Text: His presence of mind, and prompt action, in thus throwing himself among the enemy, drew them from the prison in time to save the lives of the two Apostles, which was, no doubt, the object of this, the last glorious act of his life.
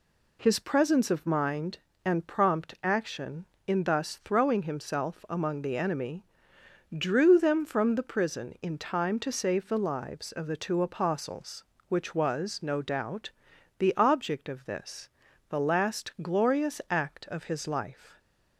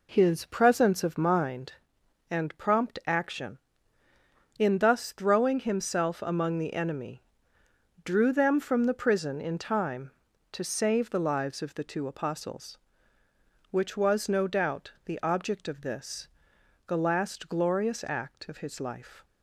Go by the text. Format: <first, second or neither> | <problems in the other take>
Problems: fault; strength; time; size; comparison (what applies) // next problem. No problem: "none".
first | starts louder than the rest; until 1.7 s; 3.5 dB